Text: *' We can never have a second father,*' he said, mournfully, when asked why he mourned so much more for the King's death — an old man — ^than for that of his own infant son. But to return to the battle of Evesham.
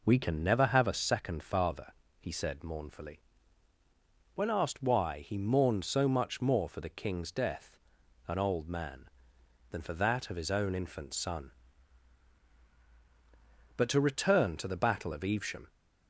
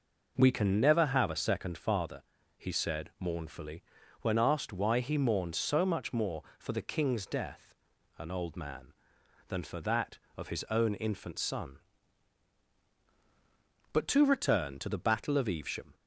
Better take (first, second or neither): neither